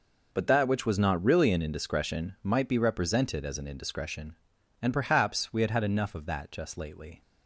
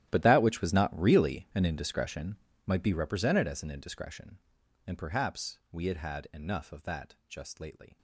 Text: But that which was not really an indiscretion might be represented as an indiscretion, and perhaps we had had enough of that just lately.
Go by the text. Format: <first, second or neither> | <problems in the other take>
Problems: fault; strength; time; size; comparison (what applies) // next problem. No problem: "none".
first | gets quieter; strong; throughout; 17.5 dB // pauses between "indiscretion" and "might"; slight; at 2.3 s; 0.28 s long